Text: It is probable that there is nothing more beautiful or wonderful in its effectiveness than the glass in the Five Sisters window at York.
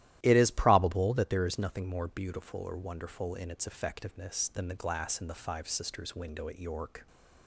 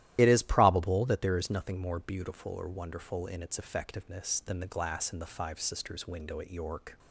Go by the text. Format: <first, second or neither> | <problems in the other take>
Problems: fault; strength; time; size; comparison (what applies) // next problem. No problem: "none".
first | loses the start of "It"; at 0.1 s; 45 ms // starts louder than the rest; strong; until 1.1 s; 13.5 dB; strong in the first